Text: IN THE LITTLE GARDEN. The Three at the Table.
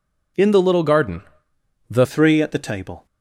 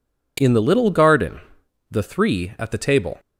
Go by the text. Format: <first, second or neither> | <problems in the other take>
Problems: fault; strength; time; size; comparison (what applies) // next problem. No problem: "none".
second | changes voice at "Three"; from 2.0 s on; 1.0 s long